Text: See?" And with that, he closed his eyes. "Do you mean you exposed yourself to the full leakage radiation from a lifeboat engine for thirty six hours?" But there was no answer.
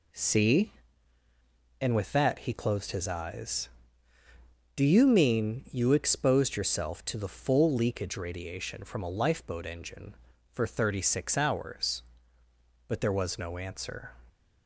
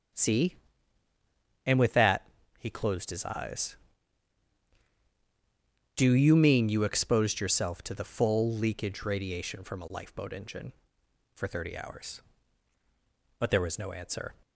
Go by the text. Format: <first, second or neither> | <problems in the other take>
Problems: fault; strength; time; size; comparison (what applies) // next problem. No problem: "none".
first | starts louder than the rest; strong; until 2.2 s; 7.5 dB // skips "six"; at 11.7 s